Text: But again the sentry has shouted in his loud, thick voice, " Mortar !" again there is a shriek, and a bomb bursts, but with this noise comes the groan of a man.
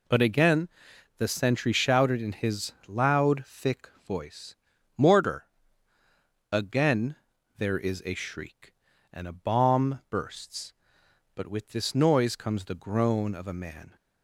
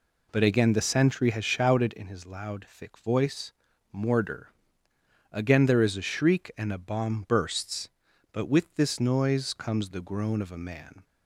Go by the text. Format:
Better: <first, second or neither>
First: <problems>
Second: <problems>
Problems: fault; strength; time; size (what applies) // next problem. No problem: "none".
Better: second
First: pauses between "again" and "the"; noticeable; at 0.6 s; 0.50 s long // skips "has"; at 1.7 s // pauses between "thick" and "voice"; slight; at 3.8 s; 0.18 s long // pauses between "again" and "there"; at 7.1 s; 0.42 s long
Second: none